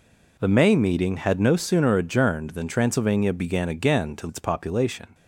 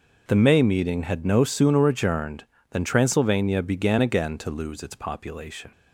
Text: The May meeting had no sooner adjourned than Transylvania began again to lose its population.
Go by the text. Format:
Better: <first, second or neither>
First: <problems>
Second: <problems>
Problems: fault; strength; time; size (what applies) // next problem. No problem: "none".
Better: second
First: skips "lose"; at 4.2 s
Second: none